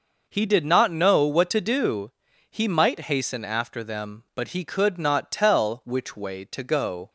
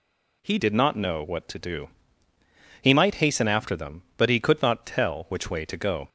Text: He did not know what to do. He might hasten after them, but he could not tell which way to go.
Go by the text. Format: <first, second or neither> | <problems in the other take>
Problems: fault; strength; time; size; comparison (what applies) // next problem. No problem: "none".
first | changes voice at "did"; from 0.5 s on; 5.5 s long